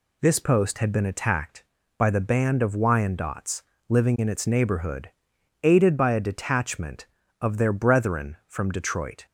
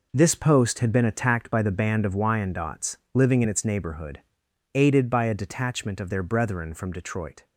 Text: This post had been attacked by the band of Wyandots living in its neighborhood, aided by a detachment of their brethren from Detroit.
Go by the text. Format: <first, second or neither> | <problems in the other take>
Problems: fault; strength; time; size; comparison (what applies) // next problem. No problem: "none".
first | gets quieter; strong; throughout; 9.5 dB // pauses between "Wyandots" and "living"; slight; at 2.9 s; 0.16 s long; slight in the first